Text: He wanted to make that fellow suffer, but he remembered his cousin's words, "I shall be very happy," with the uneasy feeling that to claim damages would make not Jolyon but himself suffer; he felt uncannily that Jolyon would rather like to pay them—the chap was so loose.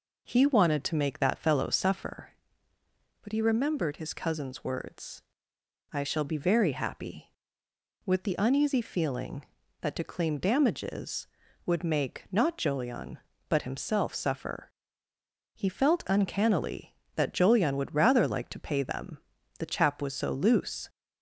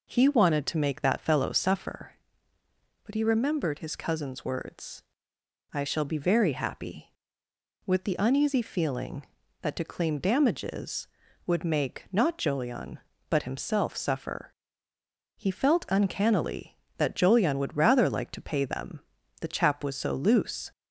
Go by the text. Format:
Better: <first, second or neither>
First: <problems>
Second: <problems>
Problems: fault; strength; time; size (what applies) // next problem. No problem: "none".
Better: neither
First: none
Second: none